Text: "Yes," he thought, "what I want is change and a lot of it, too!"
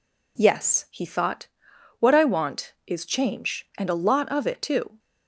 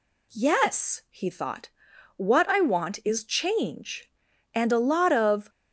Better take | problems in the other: first | stops before "it too"; at 5.4 s

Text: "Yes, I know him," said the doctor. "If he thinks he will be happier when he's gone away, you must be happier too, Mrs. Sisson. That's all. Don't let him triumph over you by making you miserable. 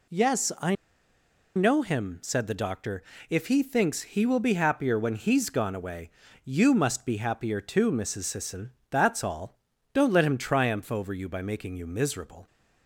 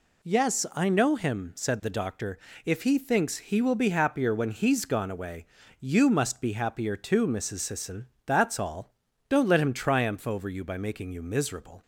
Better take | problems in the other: second | pauses between "I" and "know"; noticeable; at 0.7 s; 0.80 s long

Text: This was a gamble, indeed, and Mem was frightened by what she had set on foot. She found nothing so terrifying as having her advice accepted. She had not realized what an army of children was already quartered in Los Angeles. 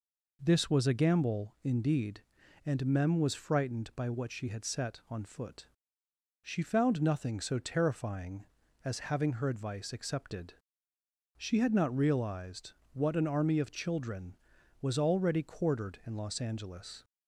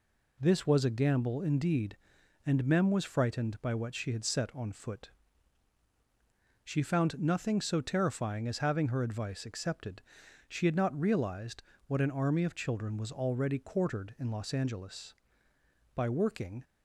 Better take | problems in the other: first | pauses between "realized" and "what"; slight; at 11.6 s; 0.26 s long; slight in the first // goes on to say "By working"; noticeable; from 15.9 s on; 0.70 s long

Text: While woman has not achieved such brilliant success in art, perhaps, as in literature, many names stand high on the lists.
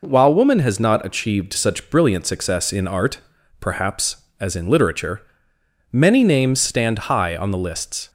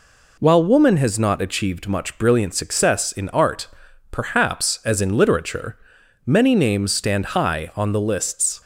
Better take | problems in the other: first | says "much" for "such"; at 1.8 s

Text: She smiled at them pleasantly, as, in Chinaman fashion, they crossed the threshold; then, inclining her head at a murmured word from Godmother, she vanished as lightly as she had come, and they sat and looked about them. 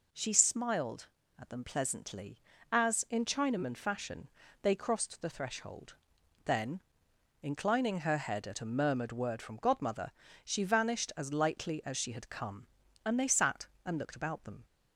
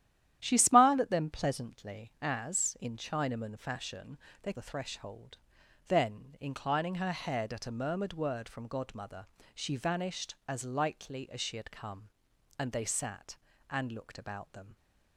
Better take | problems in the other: first | starts louder than the rest; strong; until 1.4 s; 11.5 dB // skips "crossed"; at 4.5 s

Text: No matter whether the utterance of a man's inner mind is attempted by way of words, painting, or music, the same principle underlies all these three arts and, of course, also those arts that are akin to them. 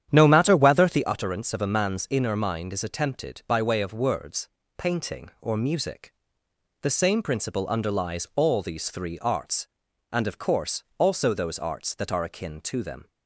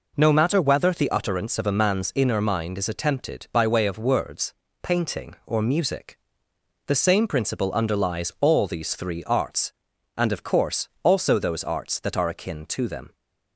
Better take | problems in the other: second | starts louder than the rest; strong; until 1.0 s; 10 dB

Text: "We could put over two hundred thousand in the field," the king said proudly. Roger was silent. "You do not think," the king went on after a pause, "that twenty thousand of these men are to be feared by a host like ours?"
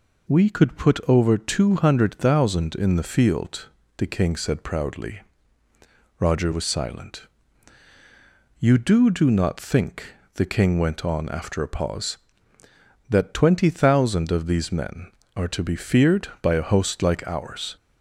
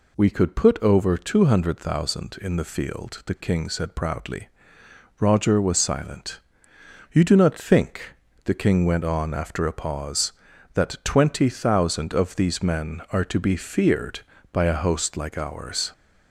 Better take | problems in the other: second | says "do" twice; at 9.1 s

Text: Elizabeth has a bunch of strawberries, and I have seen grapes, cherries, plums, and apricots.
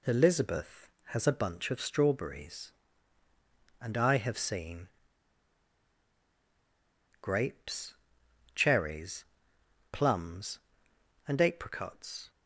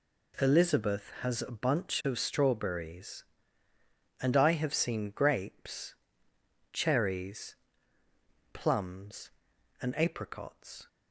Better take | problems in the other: second | pauses between "seen" and "grapes"; strong; at 4.8 s; 2.3 s long

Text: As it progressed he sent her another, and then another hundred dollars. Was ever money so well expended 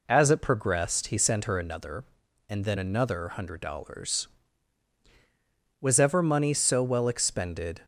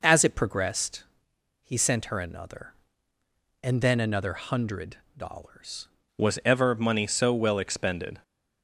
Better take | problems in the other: first | pauses between "progressed" and "he"; noticeable; at 1.0 s; 0.60 s long // pauses between "hundred" and "dollars"; slight; at 4.9 s; 0.20 s long // changes voice at "Was"; from 6.1 s on; 2.1 s long

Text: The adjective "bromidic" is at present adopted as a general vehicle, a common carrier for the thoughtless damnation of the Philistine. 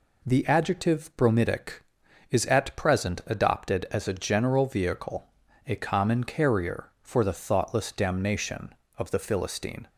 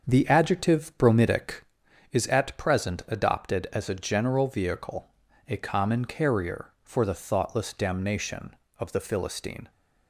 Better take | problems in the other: first | starts louder than the rest; until 1.8 s; 7 dB

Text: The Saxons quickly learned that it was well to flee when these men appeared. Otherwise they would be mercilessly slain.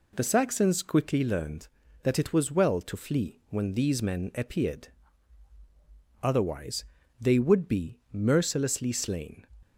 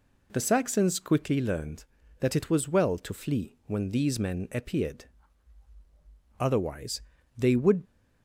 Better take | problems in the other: first | pauses between "Otherwise" and "they"; slight; at 7.0 s; 0.36 s long; slight in the first // stops before "be mercilessly slain"; at 7.8 s

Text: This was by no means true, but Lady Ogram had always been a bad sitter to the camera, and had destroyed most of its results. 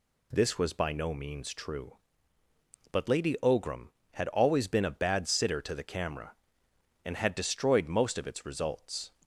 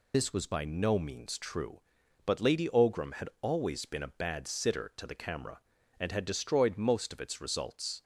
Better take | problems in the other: first | loses the start of "This"; at 0.1 s; 70 ms

